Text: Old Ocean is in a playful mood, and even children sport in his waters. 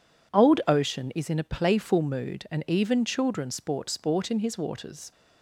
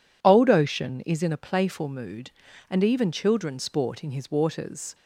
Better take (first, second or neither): second